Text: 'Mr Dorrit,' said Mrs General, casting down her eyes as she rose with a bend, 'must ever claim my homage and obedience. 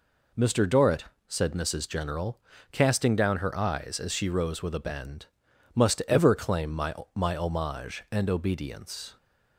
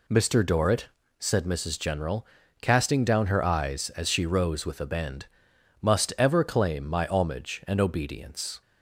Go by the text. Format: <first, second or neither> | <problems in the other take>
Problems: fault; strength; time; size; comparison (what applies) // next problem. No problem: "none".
second | says "my" twice; at 7.1 s